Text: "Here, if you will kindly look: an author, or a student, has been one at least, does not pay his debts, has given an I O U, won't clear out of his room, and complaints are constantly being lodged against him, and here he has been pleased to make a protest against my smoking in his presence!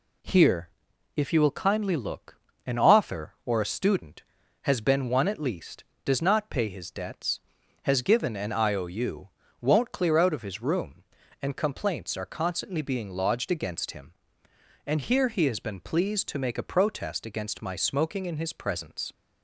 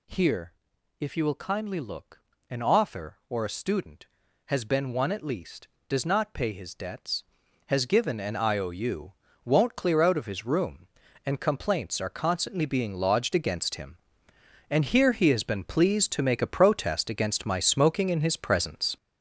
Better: first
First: none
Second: gets louder; strong; throughout; 7.5 dB

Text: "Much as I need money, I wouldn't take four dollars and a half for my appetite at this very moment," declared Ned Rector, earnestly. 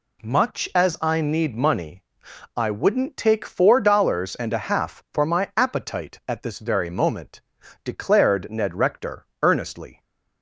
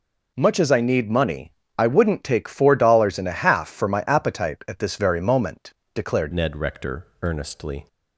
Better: first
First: none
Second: changes voice at "Ned"; from 6.3 s on; 1.5 s long

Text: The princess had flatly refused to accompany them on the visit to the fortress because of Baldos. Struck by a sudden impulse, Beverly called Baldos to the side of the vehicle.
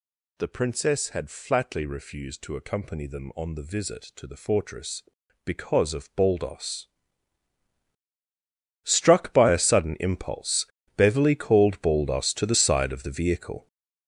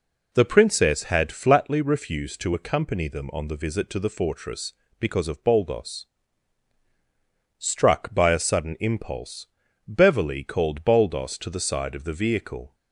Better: second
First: gets louder; strong; throughout; 8.5 dB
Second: none

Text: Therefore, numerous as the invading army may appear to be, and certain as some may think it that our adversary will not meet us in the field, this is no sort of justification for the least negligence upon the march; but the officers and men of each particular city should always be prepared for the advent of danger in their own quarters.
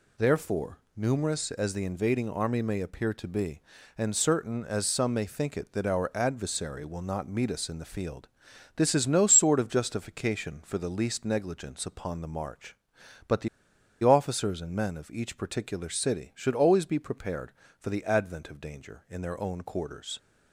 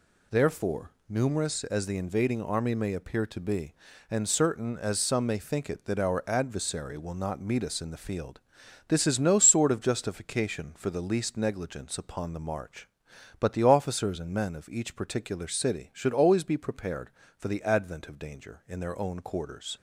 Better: second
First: pauses between "the" and "officers"; noticeable; at 13.4 s; 0.55 s long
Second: none

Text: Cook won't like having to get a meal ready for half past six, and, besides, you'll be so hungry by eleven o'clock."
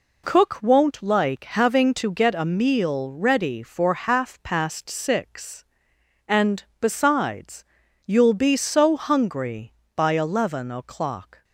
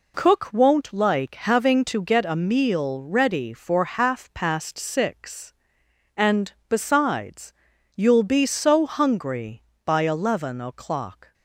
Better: neither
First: none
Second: none

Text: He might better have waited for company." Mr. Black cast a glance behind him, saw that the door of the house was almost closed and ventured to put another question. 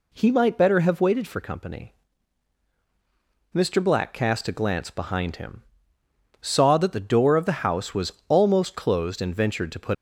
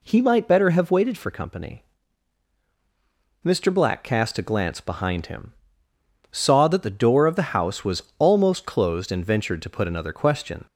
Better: second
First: pauses between "was" and "almost"; slight; at 8.1 s; 0.16 s long // stops before "another question"; at 9.9 s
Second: pauses between "was" and "almost"; slight; at 8.0 s; 0.16 s long

